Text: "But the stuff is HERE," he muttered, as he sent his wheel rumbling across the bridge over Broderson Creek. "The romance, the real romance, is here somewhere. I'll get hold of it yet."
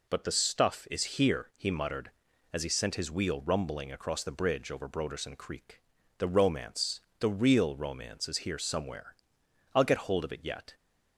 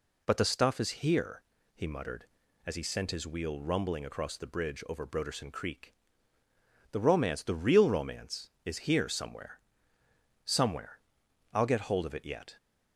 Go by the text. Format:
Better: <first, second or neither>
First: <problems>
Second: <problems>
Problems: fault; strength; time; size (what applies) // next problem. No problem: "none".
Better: first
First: none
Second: says "somewhere" twice; at 10.4 s